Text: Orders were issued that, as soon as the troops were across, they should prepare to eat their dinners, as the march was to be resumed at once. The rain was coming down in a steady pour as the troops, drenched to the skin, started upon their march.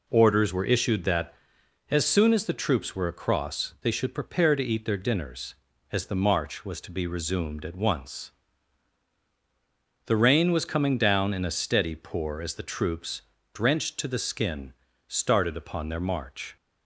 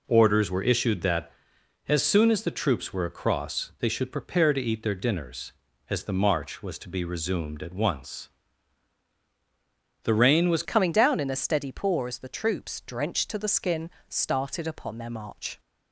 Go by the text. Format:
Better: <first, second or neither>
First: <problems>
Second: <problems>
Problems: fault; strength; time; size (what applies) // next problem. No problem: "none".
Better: first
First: none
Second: changes voice at "coming"; from 10.6 s on; 4.9 s long